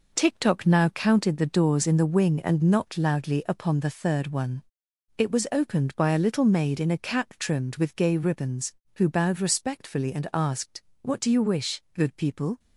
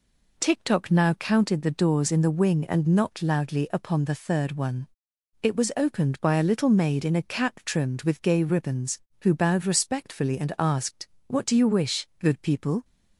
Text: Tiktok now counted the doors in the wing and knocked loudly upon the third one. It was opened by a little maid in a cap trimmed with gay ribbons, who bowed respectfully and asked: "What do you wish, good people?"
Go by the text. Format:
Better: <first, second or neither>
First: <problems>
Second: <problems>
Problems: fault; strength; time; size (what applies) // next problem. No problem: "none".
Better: second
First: gets quieter; throughout; 7 dB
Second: none